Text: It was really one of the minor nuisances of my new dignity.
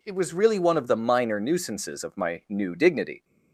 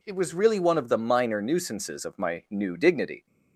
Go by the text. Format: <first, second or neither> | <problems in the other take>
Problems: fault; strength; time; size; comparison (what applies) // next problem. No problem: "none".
neither | none